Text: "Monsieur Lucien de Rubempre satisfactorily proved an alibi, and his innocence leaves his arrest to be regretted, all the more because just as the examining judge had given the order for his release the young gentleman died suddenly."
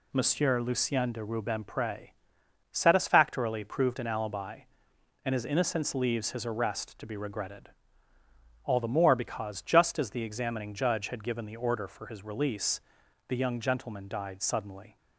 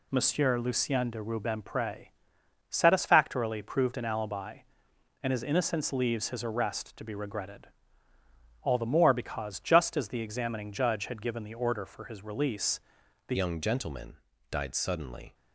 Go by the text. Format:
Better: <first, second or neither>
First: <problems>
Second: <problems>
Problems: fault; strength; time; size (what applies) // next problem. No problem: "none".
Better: first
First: pauses between "Rubempre" and "satisfactorily"; noticeable; at 2.0 s; 0.64 s long // pauses between "release" and "the"; noticeable; at 12.8 s; 0.46 s long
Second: pauses between "Rubempre" and "satisfactorily"; noticeable; at 2.0 s; 0.64 s long // pauses between "release" and "the"; noticeable; at 12.8 s; 0.46 s long // changes voice at "young"; from 13.3 s on; 2.0 s long // pauses between "gentleman" and "died"; slight; at 14.1 s; 0.32 s long